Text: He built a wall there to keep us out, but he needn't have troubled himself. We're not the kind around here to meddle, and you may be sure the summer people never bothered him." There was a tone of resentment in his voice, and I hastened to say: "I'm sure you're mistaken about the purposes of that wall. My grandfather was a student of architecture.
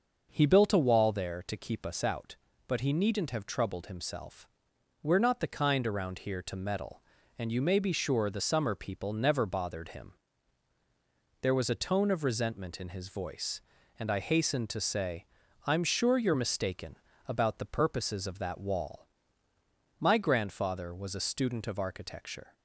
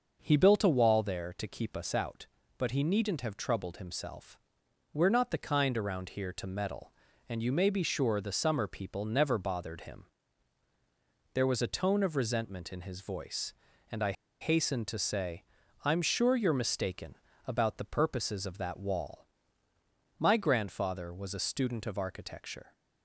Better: first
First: starts louder than the rest; noticeable; until 1.3 s; 6 dB // pauses between "mistaken" and "about"; slight; at 16.9 s; 0.30 s long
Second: starts louder than the rest; noticeable; until 1.2 s; 6 dB // pauses between "I" and "hastened"; slight; at 14.1 s; 0.28 s long // pauses between "mistaken" and "about"; slight; at 17.1 s; 0.30 s long

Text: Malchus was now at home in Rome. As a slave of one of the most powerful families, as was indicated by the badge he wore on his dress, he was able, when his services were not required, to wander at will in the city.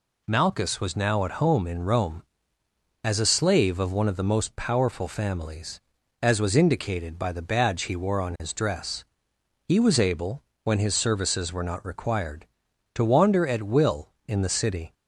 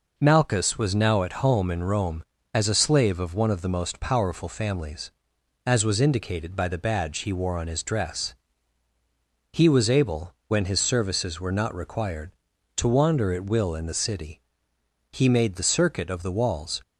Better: first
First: none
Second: goes on to say "He made the circuit of the walls"; strong; from 15.1 s on; 1.7 s long

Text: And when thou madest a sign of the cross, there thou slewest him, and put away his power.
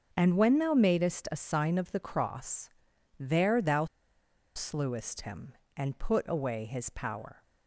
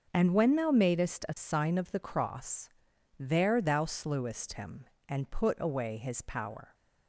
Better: second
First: starts louder than the rest; until 1.1 s; 6.5 dB // pauses between "thou" and "slewest"; noticeable; at 3.8 s; 0.70 s long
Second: starts louder than the rest; until 1.1 s; 6.5 dB

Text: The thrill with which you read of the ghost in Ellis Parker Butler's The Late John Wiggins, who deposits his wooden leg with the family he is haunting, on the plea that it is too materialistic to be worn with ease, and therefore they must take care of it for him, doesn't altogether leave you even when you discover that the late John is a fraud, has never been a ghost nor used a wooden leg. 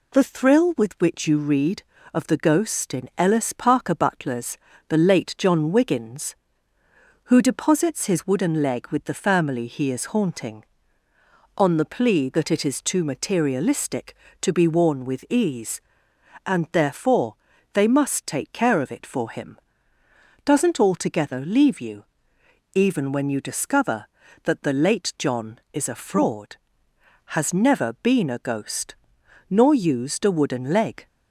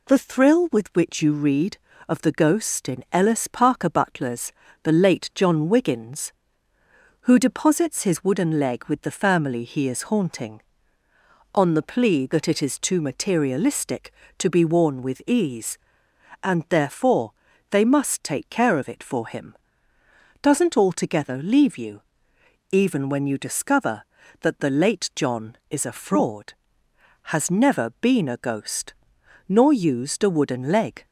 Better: neither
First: pauses between "Butler's" and "The"; slight; at 4.5 s; 0.32 s long // pauses between "therefore" and "they"; at 17.3 s; 0.40 s long // pauses between "you" and "even"; noticeable; at 22.0 s; 0.68 s long // pauses between "ghost" and "nor"; noticeable; at 28.9 s; 0.54 s long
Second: pauses between "Butler's" and "The"; slight; at 4.5 s; 0.32 s long // pauses between "therefore" and "they"; at 17.3 s; 0.40 s long // pauses between "you" and "even"; noticeable; at 22.0 s; 0.68 s long // pauses between "ghost" and "nor"; noticeable; at 28.9 s; 0.54 s long

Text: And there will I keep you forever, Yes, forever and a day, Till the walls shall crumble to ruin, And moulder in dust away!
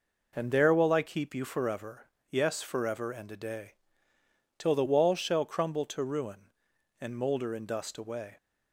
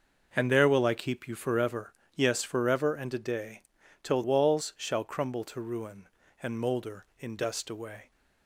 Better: first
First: none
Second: skips "the"; at 4.2 s

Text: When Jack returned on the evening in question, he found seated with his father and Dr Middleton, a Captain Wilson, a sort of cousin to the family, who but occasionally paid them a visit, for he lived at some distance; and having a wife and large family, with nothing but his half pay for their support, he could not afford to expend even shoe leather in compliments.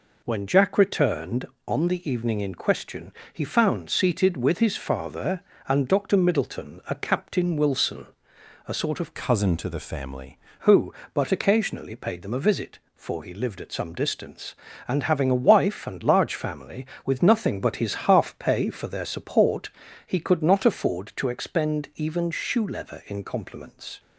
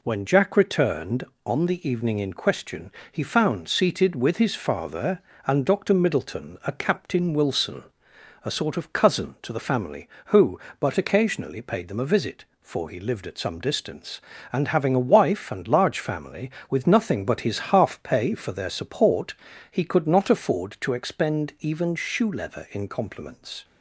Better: second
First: changes voice from "cousin" to "family"; from 9.1 to 10.3 s; 1.2 s long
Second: none

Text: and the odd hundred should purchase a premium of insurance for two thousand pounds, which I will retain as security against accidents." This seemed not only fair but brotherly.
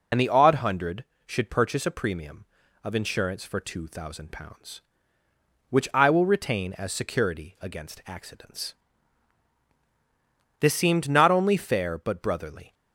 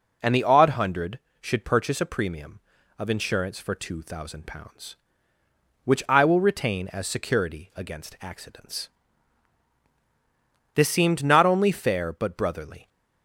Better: second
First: loses the start of "and"; at 0.1 s; 45 ms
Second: none

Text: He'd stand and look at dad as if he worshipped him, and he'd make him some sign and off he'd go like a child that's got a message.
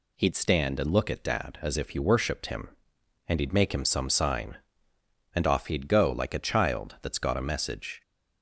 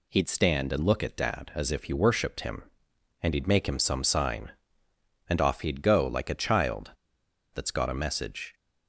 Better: first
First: none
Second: pauses between "child" and "that's"; noticeable; at 6.9 s; 0.63 s long

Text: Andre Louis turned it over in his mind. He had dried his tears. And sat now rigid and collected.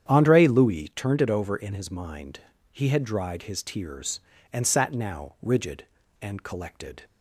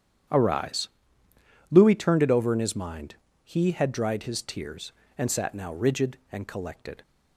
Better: first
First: starts louder than the rest; strong; until 1.1 s; 9 dB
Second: starts louder than the rest; strong; until 2.1 s; 9.5 dB // says "Arise" for "Andre"; at 0.2 s

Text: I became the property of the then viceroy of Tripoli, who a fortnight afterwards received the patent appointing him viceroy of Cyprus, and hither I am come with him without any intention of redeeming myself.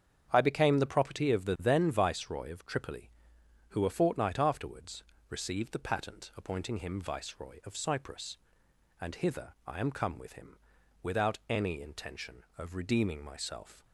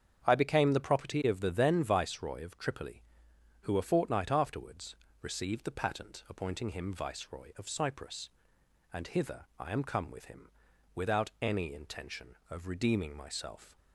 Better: neither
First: starts louder than the rest; strong; until 1.3 s; 7.5 dB // pauses between "afterwards" and "received"; slight; at 5.0 s; 0.24 s long // pauses between "him" and "without"; noticeable; at 10.5 s; 0.46 s long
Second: starts louder than the rest; strong; until 1.2 s; 7.5 dB // pauses between "afterwards" and "received"; slight; at 4.9 s; 0.24 s long // pauses between "him" and "without"; noticeable; at 10.4 s; 0.46 s long

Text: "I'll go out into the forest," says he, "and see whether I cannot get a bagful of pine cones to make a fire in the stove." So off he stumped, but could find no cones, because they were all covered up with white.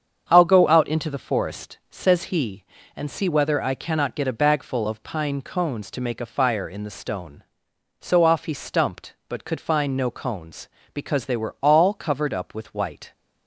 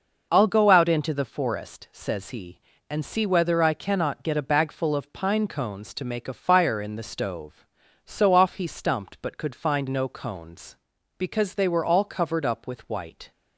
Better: second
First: starts louder than the rest; strong; until 1.2 s; 7.5 dB // says "stone" for "stove"; at 6.9 s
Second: none

